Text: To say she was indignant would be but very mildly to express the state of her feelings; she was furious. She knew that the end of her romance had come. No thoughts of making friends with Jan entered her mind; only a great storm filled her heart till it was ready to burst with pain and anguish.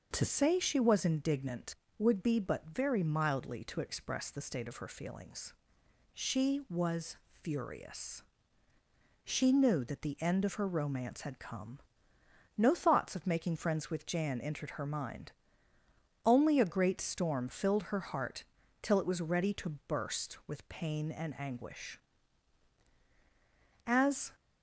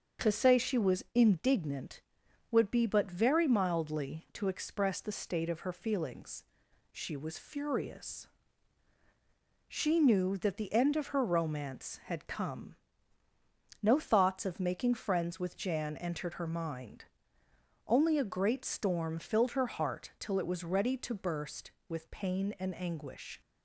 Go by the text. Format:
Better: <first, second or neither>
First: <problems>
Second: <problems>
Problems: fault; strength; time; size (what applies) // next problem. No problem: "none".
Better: second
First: starts louder than the rest; until 1.1 s; 6 dB // pauses between "heart" and "till"; at 18.4 s; 0.38 s long // goes on to say "As"; slight; from 23.8 s on; 0.46 s long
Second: starts louder than the rest; until 1.3 s; 6.5 dB